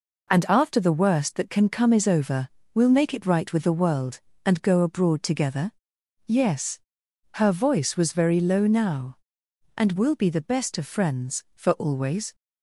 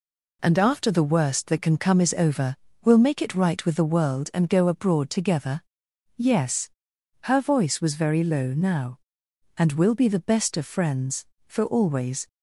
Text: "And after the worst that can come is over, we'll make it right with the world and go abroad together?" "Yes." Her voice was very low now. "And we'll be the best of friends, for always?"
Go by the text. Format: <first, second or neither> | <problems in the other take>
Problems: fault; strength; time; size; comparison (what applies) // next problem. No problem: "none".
neither | none